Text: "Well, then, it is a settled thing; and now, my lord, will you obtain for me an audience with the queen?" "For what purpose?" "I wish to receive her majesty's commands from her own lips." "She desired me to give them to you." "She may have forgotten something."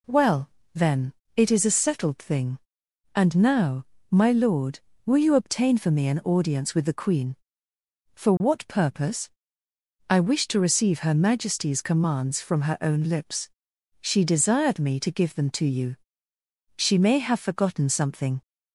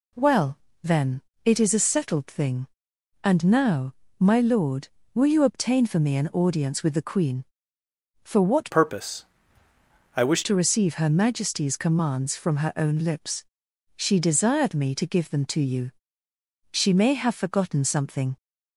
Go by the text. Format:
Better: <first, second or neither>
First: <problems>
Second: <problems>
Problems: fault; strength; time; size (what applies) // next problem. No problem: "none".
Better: first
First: none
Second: changes voice from "purpose" to "wish"; from 8.7 to 10.4 s; 1.7 s long